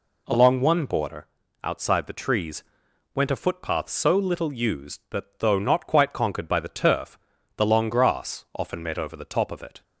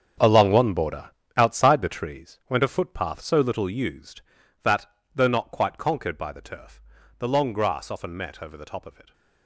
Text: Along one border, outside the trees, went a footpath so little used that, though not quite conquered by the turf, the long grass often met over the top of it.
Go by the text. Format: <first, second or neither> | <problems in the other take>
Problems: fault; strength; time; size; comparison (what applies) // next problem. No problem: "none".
first | gets quieter; strong; throughout; 13 dB